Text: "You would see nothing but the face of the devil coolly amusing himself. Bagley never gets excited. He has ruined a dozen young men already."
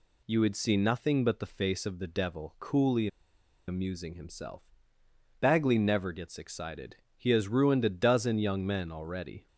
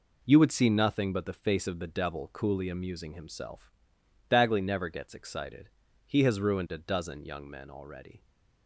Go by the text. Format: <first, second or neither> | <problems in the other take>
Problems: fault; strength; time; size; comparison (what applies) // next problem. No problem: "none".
second | pauses between "coolly" and "amusing"; noticeable; at 3.0 s; 0.60 s long